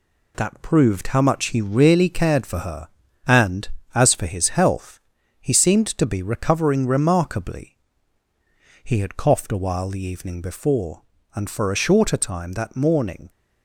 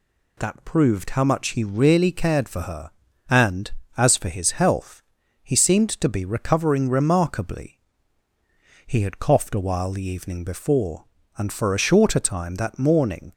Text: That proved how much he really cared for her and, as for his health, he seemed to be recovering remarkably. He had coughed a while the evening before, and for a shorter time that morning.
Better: second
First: gets quieter; noticeable; throughout; 4.5 dB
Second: none

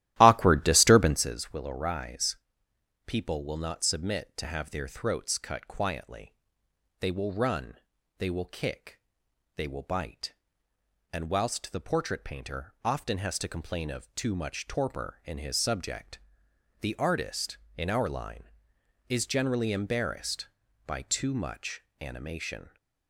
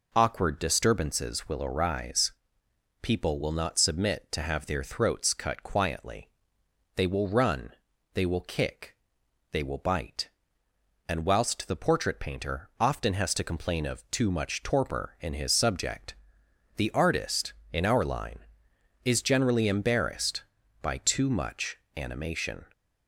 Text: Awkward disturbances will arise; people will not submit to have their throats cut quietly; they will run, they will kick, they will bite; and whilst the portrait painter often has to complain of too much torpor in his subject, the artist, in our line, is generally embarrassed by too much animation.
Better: second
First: starts louder than the rest; strong; until 1.4 s; 14.5 dB // pauses between "much" and "animation"; slight; at 21.8 s; 0.18 s long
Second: pauses between "much" and "animation"; slight; at 21.7 s; 0.18 s long

